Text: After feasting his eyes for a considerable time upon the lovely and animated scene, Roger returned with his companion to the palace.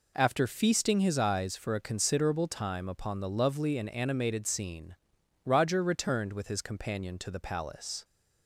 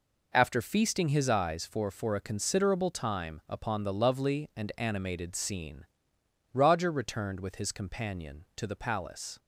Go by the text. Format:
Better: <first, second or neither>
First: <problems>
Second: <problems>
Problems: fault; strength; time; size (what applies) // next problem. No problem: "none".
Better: first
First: none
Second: says "for" twice; at 1.9 s